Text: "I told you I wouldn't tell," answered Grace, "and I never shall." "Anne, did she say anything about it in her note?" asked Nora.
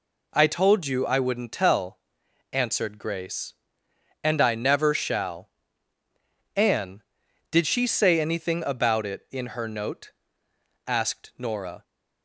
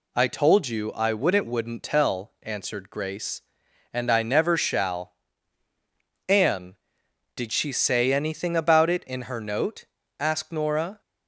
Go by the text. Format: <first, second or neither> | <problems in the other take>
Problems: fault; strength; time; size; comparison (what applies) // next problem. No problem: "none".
first | says "wouldn't" twice; at 1.4 s